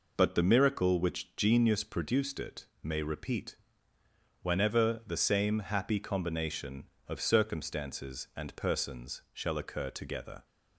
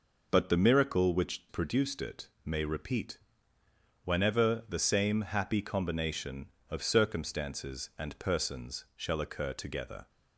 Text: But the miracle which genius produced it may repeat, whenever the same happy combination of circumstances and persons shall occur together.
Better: first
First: pauses between "it" and "may"; slight; at 2.6 s; 0.16 s long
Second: skips "genius"; at 1.4 s // pauses between "it" and "may"; slight; at 2.2 s; 0.16 s long

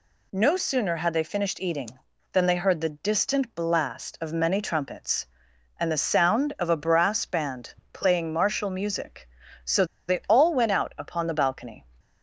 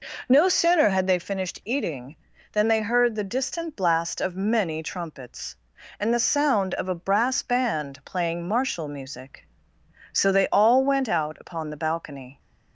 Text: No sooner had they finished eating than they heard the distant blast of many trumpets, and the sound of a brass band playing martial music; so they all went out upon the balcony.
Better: second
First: pauses between "band" and "playing"; slight; at 7.7 s; 0.20 s long // pauses between "so" and "they"; slight; at 9.8 s; 0.22 s long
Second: none

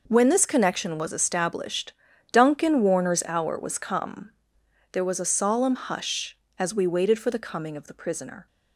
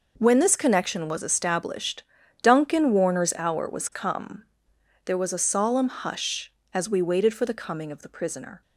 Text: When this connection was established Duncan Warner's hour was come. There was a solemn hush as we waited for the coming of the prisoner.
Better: neither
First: pauses between "established" and "Duncan"; at 1.9 s; 0.38 s long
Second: pauses between "established" and "Duncan"; at 2.0 s; 0.38 s long

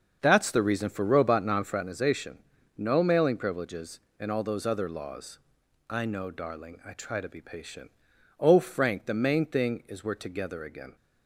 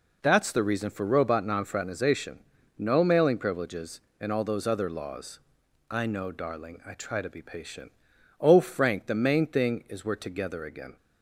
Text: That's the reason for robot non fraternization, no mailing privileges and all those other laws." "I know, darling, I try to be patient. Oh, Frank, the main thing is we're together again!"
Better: second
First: starts louder than the rest; until 1.8 s; 7 dB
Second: none

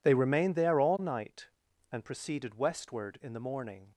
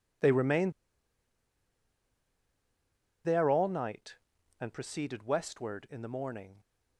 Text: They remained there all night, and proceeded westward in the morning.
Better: first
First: none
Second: pauses between "remained" and "there"; strong; at 0.7 s; 2.5 s long

